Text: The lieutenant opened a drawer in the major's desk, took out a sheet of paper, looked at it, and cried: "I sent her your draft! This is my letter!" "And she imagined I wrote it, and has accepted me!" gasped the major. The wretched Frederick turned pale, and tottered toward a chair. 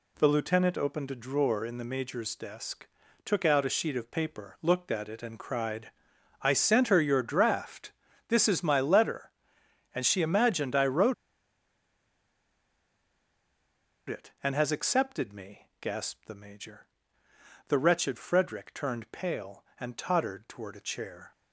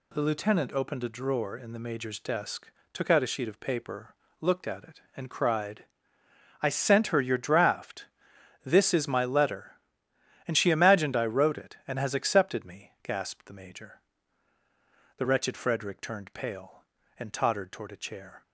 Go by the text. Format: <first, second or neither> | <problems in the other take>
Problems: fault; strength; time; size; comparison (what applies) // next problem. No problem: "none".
second | pauses between "wrote" and "it"; strong; at 11.1 s; 2.9 s long